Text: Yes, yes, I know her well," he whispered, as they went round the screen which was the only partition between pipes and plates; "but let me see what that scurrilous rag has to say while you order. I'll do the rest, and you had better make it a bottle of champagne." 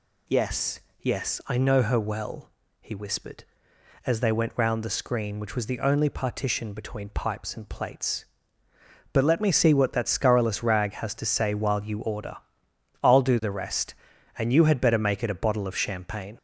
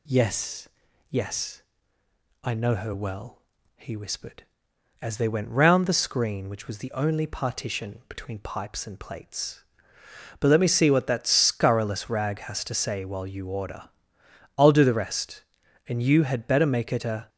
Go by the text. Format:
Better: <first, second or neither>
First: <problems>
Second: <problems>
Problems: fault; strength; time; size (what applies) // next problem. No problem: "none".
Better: first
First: none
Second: stops before "bottle of champagne"; at 17.2 s